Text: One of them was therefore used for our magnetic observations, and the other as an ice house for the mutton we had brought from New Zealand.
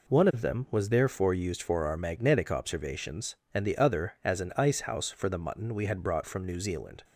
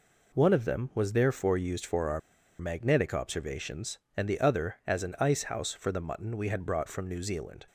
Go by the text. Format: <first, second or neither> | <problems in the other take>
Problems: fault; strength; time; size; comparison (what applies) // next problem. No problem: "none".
first | pauses between "our" and "magnetic"; at 2.2 s; 0.39 s long